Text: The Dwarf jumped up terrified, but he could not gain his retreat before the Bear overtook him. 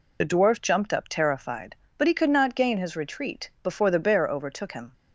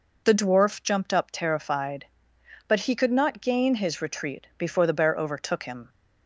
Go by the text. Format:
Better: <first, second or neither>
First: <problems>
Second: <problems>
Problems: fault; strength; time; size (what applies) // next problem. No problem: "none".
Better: second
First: loses the start of "The"; at 0.2 s; 35 ms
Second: none